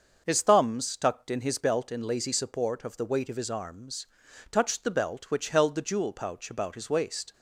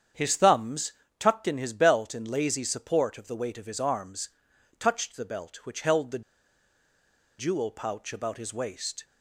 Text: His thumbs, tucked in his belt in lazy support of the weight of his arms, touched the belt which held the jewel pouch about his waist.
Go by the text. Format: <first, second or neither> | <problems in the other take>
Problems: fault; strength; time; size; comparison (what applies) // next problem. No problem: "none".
first | starts louder than the rest; strong; until 1.4 s; 8 dB; also in the first // pauses between "the" and "jewel"; at 6.2 s; 1.1 s long